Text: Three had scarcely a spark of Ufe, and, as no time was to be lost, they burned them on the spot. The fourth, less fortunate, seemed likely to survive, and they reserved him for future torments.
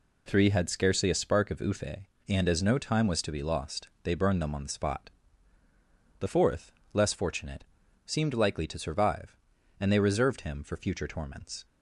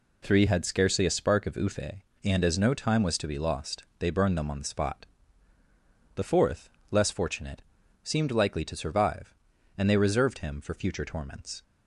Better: neither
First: none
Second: none

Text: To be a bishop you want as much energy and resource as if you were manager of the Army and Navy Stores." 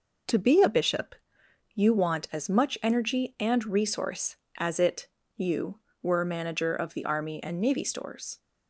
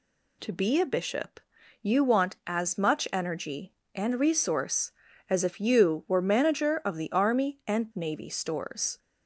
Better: second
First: pauses between "bishop" and "you"; noticeable; at 1.1 s; 0.60 s long // says "it" for "if"; at 4.7 s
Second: pauses between "bishop" and "you"; at 1.3 s; 0.42 s long

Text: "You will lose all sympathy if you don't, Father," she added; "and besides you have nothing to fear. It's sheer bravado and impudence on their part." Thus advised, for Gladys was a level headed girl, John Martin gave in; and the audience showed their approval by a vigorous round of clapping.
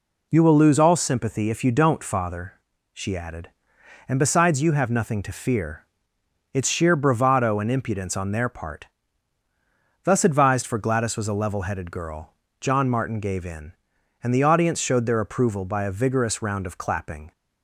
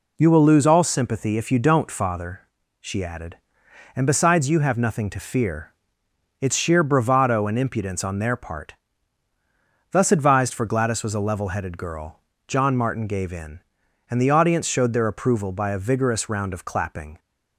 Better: neither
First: none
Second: none

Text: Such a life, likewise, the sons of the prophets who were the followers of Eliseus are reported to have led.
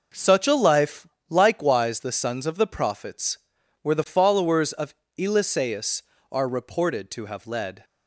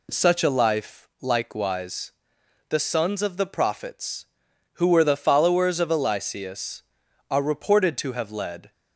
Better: second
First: skips "who"; at 3.6 s // pauses between "of" and "Eliseus"; slight; at 4.9 s; 0.24 s long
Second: none

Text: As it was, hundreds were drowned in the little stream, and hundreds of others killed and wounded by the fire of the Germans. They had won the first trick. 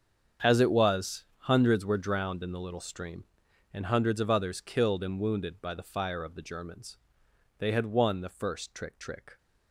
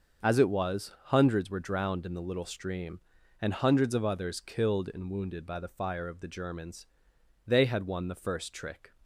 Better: second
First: starts louder than the rest; strong; until 1.6 s; 7.5 dB // says "trick" twice; at 8.9 s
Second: starts louder than the rest; noticeable; until 1.3 s; 6 dB

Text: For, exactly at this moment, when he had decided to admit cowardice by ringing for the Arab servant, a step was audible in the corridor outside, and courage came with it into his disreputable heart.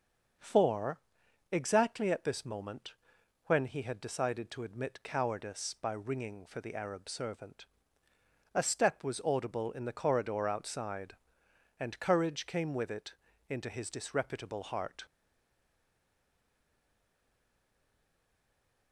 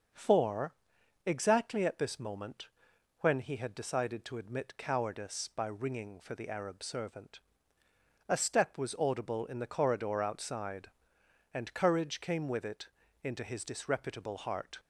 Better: second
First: starts louder than the rest; noticeable; until 1.9 s; 6 dB // pauses between "it" and "into"; slight; at 13.1 s; 0.34 s long // stays silent after the last word; strong; from 15.0 s on; 3.9 s long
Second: starts louder than the rest; noticeable; until 1.6 s; 6 dB // pauses between "it" and "into"; slight; at 12.8 s; 0.34 s long

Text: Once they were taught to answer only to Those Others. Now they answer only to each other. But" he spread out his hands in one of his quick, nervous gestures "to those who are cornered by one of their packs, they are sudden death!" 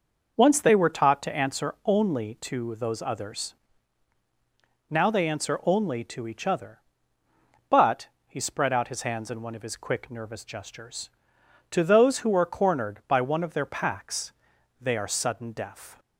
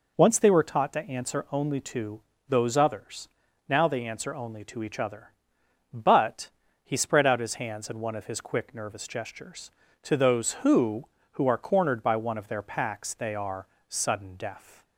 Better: first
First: pauses between "But" and "he"; slight; at 8.0 s; 0.20 s long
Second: pauses between "to" and "Those"; slight; at 2.2 s; 0.28 s long // pauses between "But" and "he"; slight; at 6.5 s; 0.34 s long // says "who" twice; at 11.3 s // pauses between "are" and "sudden"; slight; at 13.6 s; 0.22 s long

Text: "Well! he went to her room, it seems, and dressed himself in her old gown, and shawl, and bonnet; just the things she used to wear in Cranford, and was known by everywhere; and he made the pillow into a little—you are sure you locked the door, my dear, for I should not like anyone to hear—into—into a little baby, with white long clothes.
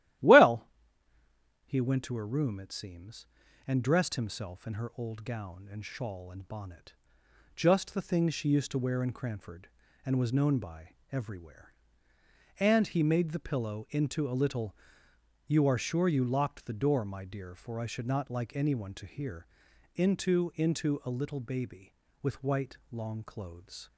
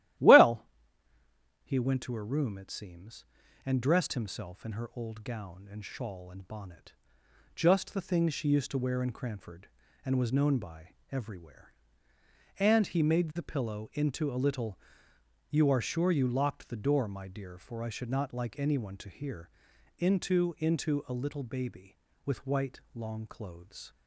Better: neither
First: starts louder than the rest; strong; until 2.2 s; 13.5 dB // pauses between "by" and "everywhere"; slight; at 10.9 s; 0.16 s long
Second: starts louder than the rest; strong; until 2.1 s; 13.5 dB // pauses between "by" and "everywhere"; slight; at 10.9 s; 0.16 s long

